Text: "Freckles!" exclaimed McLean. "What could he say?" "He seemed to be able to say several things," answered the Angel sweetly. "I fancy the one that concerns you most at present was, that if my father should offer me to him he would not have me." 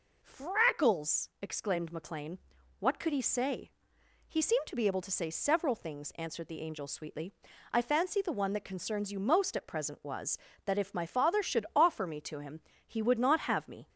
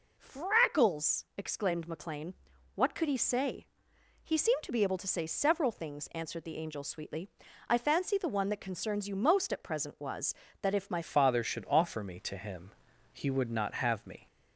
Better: first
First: pauses between "him" and "he"; slight; at 12.6 s; 0.26 s long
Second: changes voice at "father"; from 11.0 s on; 3.2 s long // pauses between "him" and "he"; at 12.7 s; 0.40 s long

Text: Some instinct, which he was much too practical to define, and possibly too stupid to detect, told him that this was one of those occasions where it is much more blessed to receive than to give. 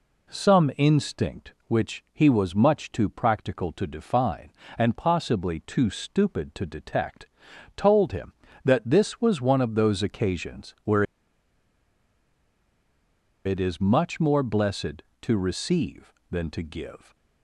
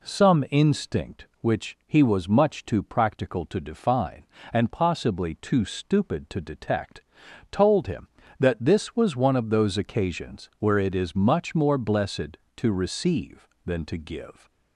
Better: second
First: pauses between "where" and "it"; strong; at 11.0 s; 2.4 s long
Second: none

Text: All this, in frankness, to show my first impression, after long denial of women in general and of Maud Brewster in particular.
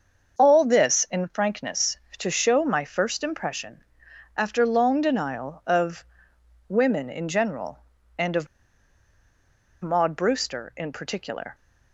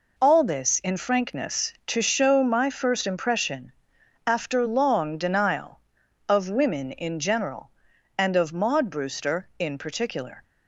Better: second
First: starts louder than the rest; until 1.3 s; 6.5 dB // pauses between "of" and "women"; noticeable; at 6.0 s; 0.64 s long // pauses between "of" and "Maud"; strong; at 8.4 s; 1.3 s long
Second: none

